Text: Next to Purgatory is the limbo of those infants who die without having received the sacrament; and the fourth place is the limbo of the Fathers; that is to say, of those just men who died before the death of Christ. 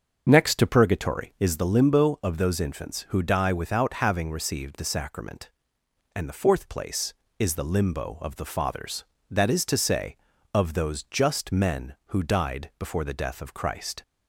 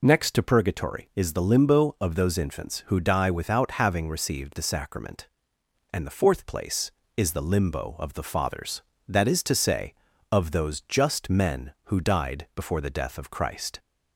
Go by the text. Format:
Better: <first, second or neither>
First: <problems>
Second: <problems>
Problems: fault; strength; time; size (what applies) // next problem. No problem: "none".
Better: second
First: starts louder than the rest; until 1.7 s; 6.5 dB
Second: none